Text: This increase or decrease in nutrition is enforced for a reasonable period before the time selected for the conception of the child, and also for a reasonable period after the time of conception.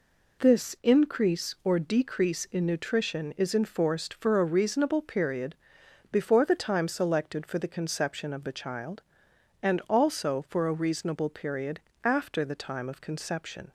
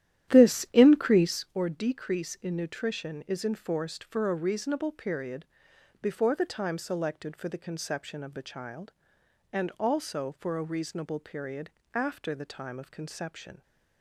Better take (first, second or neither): first